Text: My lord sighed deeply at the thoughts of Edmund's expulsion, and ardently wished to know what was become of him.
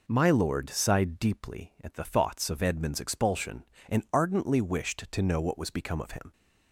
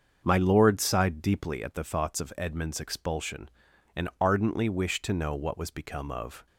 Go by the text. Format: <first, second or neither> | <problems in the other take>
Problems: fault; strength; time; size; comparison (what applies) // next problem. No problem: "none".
first | starts louder than the rest; until 1.2 s; 6.5 dB // stops before "him"; at 6.4 s